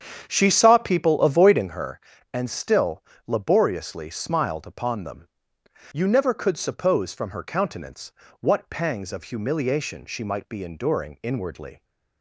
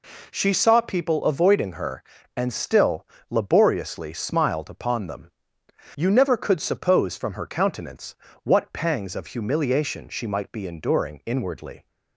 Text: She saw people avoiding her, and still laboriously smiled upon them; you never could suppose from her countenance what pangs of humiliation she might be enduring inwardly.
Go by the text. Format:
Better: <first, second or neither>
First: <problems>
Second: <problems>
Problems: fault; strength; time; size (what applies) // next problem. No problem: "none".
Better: second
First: starts louder than the rest; strong; until 1.8 s; 8.5 dB // pauses between "still" and "laboriously"; slight; at 3.0 s; 0.24 s long // pauses between "countenance" and "what"; slight; at 8.1 s; 0.28 s long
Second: pauses between "still" and "laboriously"; slight; at 3.0 s; 0.24 s long // pauses between "countenance" and "what"; slight; at 8.1 s; 0.28 s long